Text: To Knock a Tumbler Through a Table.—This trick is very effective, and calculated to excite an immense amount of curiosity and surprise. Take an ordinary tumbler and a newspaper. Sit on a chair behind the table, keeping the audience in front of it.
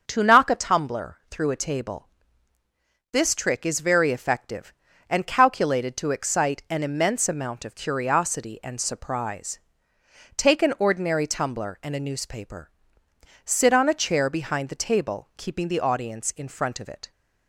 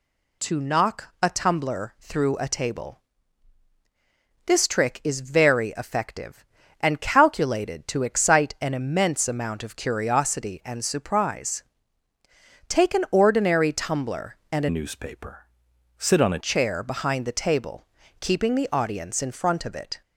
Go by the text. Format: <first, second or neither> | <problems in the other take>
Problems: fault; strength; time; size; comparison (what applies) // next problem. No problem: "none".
first | changes voice from "newspaper" to "a"; from 14.7 to 16.3 s; 1.6 s long